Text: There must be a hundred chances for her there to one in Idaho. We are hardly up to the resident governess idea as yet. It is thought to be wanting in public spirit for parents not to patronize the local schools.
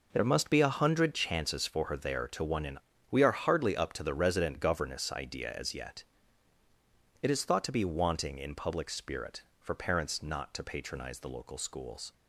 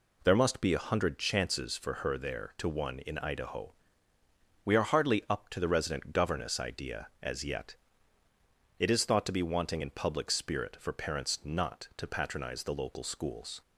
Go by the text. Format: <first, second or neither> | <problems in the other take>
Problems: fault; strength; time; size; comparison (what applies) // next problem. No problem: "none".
second | skips "Idaho"; at 2.9 s